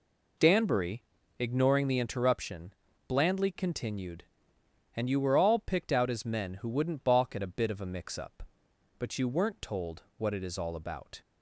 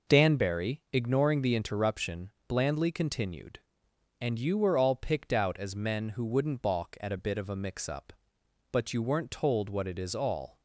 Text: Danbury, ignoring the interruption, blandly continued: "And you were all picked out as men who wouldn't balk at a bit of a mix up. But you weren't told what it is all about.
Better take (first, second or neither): first